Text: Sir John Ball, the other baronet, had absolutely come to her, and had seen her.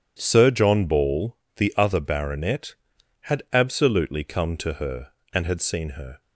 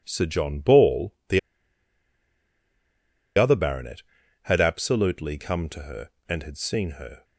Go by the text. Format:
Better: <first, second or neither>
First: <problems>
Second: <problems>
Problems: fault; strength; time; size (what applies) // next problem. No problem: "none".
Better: first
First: none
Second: pauses between "the" and "other"; strong; at 1.3 s; 1.9 s long